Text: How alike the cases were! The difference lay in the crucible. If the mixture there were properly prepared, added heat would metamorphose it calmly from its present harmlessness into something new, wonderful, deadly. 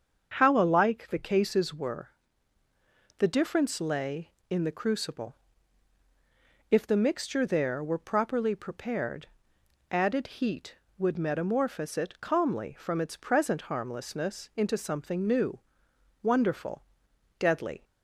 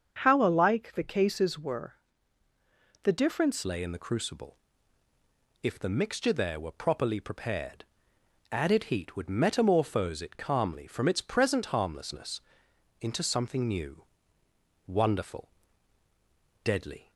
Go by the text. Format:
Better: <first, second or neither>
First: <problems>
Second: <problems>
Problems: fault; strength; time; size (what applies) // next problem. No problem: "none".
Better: first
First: starts louder than the rest; until 1.3 s; 7 dB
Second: starts louder than the rest; until 1.2 s; 7 dB // changes voice at "lay"; from 3.6 s on; 13.5 s long // pauses between "harmlessness" and "into"; noticeable; at 12.4 s; 0.58 s long